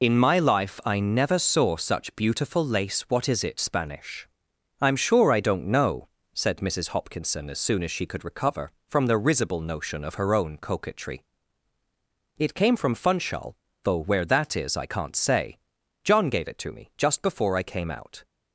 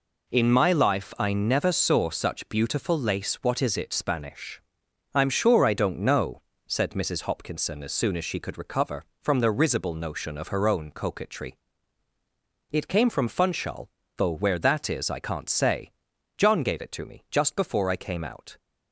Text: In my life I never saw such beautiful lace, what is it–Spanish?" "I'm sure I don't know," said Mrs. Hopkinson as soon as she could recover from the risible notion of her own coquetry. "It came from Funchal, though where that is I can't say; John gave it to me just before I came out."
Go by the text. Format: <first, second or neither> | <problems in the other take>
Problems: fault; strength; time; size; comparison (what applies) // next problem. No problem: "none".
second | loses the start of "In"; at 0.0 s; 55 ms